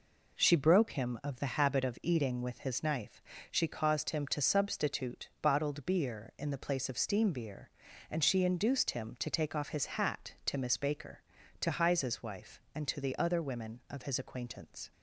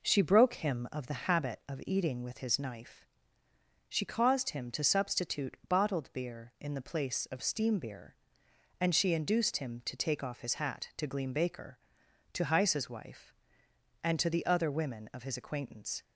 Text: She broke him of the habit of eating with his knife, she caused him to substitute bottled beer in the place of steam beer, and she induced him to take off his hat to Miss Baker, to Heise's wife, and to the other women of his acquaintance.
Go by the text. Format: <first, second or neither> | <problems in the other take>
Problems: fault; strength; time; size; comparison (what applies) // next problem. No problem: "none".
first | says "Gleam" for "Miss"; at 11.0 s